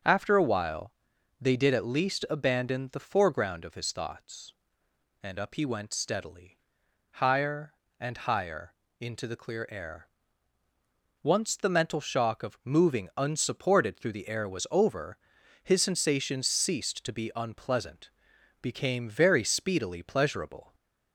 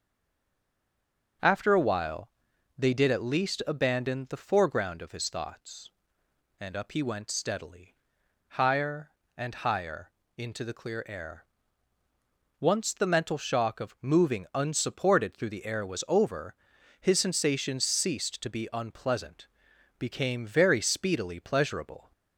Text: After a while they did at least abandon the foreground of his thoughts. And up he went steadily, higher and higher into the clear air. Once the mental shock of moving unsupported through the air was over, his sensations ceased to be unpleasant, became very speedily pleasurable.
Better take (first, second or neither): first